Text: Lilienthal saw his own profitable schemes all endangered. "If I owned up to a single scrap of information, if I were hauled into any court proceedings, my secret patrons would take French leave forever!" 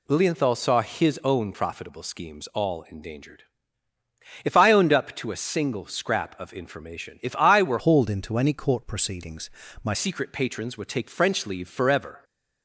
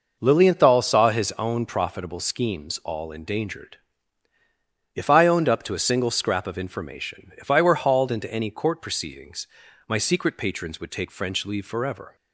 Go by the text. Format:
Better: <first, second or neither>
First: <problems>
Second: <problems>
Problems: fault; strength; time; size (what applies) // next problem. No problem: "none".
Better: second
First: changes voice from "hauled" to "my"; from 7.7 to 9.9 s; 2.2 s long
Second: none